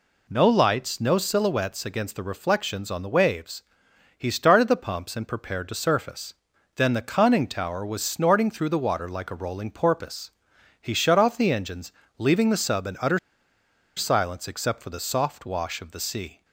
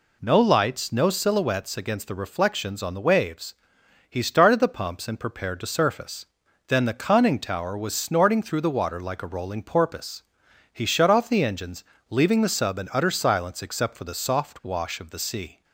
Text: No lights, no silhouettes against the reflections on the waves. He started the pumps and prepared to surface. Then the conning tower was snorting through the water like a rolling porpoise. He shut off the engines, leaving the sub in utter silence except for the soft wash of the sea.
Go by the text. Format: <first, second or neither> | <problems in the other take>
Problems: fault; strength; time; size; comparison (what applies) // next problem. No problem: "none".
second | pauses between "utter" and "silence"; noticeable; at 13.1 s; 0.77 s long